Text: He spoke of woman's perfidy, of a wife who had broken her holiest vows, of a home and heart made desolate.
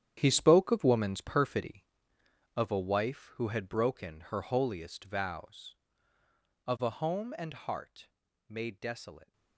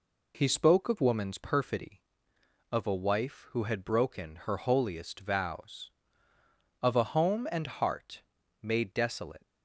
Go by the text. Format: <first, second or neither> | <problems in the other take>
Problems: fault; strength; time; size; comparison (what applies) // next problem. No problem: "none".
second | gets quieter; strong; throughout; 14 dB // pauses between "heart" and "made"; slight; at 8.1 s; 0.36 s long; slight in the second